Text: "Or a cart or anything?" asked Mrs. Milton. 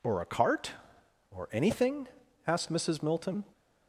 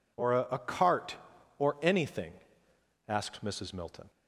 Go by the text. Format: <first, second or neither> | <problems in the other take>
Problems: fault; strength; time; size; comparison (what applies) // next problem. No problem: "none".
first | says "a" twice; at 0.5 s